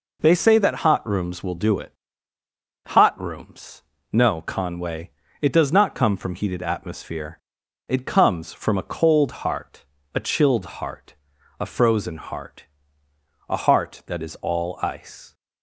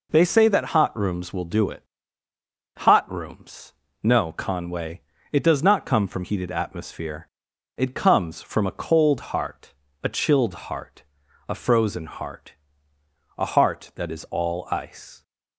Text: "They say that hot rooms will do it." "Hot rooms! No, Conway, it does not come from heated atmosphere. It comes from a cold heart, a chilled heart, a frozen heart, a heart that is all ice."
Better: neither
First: none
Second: none

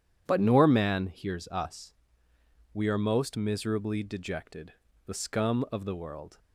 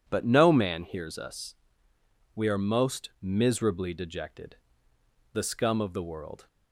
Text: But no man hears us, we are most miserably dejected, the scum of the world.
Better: second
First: says "nor" for "no"; at 0.4 s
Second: none

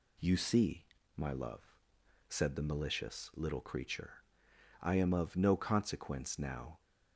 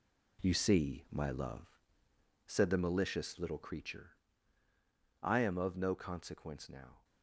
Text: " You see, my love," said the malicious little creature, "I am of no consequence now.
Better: first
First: none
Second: gets quieter; strong; throughout; 9.5 dB

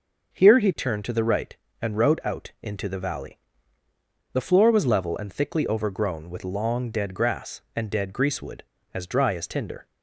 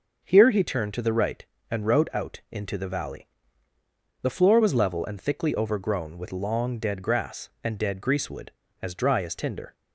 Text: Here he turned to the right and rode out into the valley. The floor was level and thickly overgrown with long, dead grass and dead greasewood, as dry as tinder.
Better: neither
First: starts louder than the rest; until 1.3 s; 6 dB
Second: starts louder than the rest; until 1.2 s; 6 dB

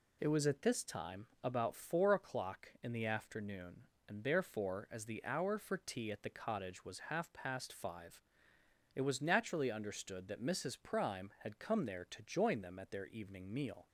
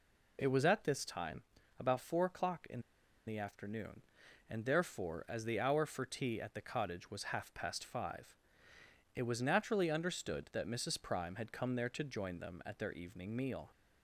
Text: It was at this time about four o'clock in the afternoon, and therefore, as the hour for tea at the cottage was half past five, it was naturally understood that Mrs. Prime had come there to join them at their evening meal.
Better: first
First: none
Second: pauses between "time" and "about"; slight; at 1.4 s; 0.36 s long // pauses between "in" and "the"; noticeable; at 2.7 s; 0.46 s long

